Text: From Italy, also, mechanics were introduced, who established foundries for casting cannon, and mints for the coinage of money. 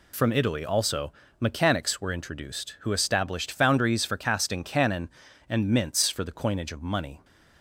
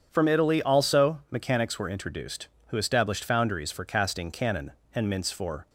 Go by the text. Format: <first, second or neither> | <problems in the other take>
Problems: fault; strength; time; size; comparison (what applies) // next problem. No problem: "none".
first | starts louder than the rest; strong; until 1.1 s; 8 dB // stops before "the coinage of money"; at 5.6 s